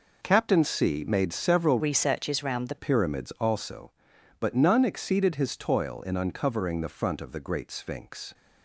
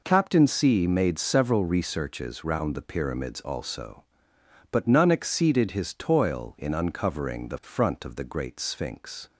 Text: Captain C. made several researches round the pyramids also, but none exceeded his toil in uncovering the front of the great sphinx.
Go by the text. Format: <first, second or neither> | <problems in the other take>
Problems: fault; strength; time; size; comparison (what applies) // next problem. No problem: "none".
second | changes voice from "researches" to "the"; from 1.7 to 2.7 s; 1.0 s long